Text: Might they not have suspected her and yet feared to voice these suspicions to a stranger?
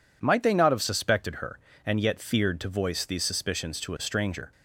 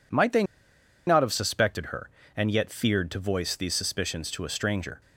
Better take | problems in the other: first | pauses between "they" and "not"; noticeable; at 0.4 s; 0.63 s long

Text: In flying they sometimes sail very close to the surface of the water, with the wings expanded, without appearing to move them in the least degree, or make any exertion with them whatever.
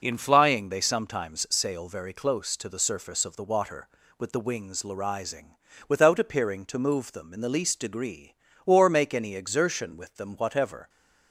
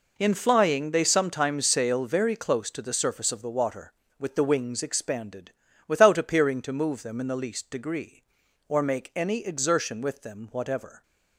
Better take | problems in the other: second | says "larising" for "expanded"; at 4.8 s

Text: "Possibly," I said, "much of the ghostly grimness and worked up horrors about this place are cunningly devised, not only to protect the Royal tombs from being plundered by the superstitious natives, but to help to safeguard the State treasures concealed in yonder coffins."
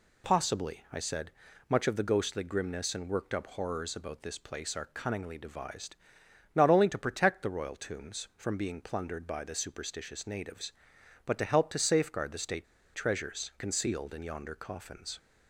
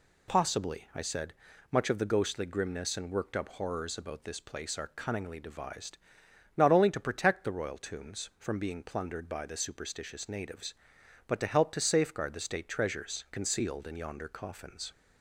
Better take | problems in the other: second | pauses between "State" and "treasures"; slight; at 12.6 s; 0.28 s long

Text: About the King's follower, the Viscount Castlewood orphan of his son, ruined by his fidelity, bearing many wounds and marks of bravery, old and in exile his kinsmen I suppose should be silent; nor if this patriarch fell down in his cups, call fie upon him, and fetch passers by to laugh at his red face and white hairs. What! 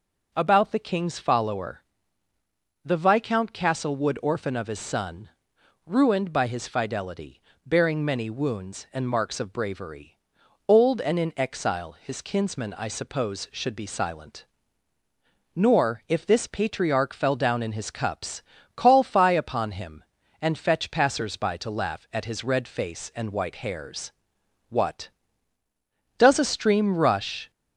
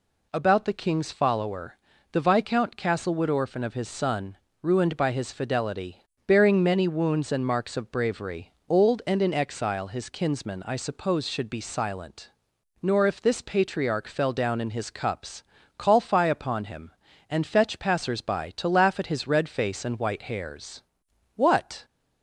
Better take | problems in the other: second | goes on to say "does a stream rush"; from 26.1 s on; 1.3 s long

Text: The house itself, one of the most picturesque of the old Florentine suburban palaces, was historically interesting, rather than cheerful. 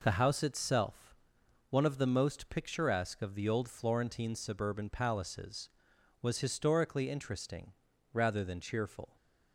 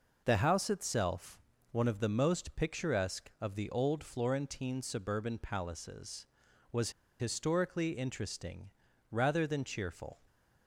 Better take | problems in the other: first | pauses between "was" and "historically"; slight; at 6.9 s; 0.29 s long

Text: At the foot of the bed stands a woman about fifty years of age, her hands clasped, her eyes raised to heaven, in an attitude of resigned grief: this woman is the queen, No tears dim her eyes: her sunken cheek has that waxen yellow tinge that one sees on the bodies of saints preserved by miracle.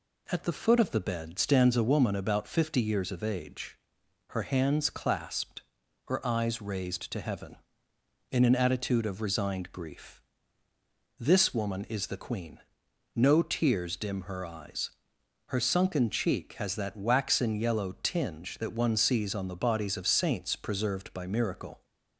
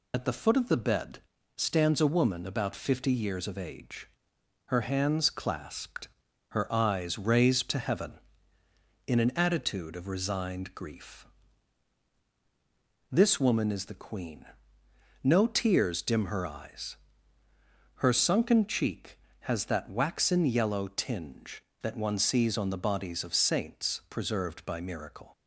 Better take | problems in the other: first | loses the start of "At"; at 0.1 s; 40 ms // pauses between "bed" and "stands"; at 1.1 s; 0.38 s long

